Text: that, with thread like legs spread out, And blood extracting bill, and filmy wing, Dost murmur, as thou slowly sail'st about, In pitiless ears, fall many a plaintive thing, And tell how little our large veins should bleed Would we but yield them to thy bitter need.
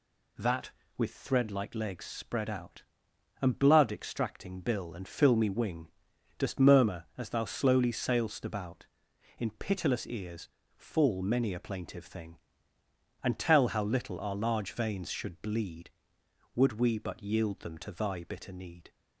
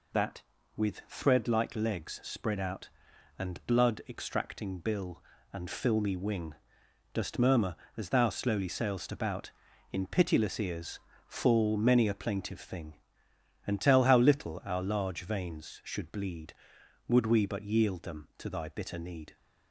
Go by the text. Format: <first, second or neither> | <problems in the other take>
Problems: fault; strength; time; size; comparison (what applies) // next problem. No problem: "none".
neither | none